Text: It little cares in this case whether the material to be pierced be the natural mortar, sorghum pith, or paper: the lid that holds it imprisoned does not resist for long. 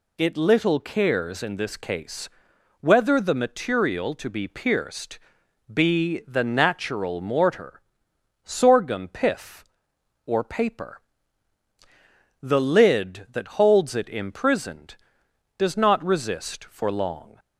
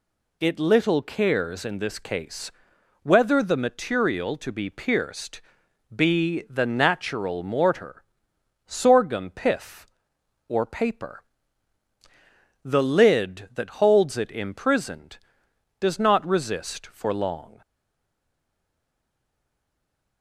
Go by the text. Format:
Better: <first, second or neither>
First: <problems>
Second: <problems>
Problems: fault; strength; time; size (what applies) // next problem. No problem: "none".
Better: first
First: pauses between "case" and "whether"; noticeable; at 2.2 s; 0.52 s long // pauses between "pierced" and "be"; noticeable; at 5.1 s; 0.56 s long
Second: pauses between "case" and "whether"; noticeable; at 2.5 s; 0.52 s long // pauses between "pierced" and "be"; noticeable; at 5.3 s; 0.56 s long // stays silent after the last word; strong; from 17.6 s on; 2.6 s long